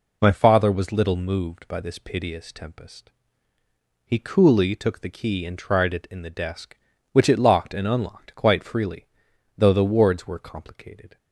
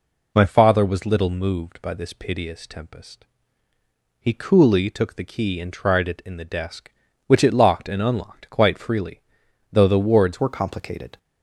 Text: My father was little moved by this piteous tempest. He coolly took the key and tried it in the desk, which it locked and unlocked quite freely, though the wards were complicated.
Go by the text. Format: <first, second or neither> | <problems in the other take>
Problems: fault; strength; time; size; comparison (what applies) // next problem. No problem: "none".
first | changes voice at "were"; from 10.3 s on; 0.8 s long